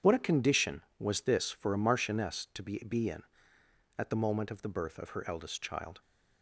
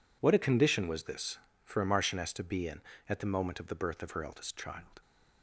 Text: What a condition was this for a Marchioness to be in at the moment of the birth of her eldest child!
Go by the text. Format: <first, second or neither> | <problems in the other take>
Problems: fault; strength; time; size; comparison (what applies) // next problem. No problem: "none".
second | says "be" twice; at 2.8 s